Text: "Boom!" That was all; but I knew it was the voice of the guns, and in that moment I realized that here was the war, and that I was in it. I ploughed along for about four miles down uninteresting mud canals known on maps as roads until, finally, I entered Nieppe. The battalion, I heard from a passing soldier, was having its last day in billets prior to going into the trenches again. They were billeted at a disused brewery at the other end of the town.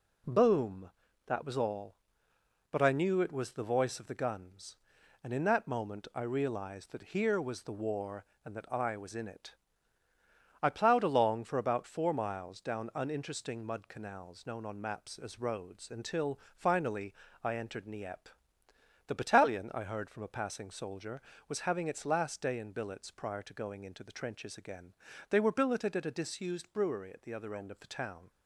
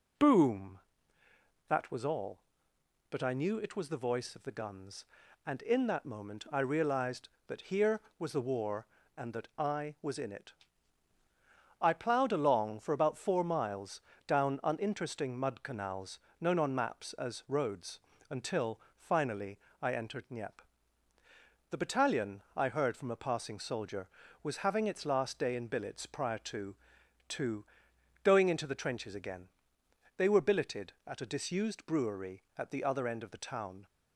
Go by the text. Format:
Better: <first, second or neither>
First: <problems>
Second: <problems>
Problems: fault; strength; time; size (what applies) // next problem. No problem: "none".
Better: first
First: none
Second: pauses between "miles" and "down"; slight; at 13.9 s; 0.26 s long // pauses between "canals" and "known"; slight; at 16.1 s; 0.22 s long // pauses between "roads" and "until"; slight; at 17.9 s; 0.30 s long // says "to" twice; at 27.2 s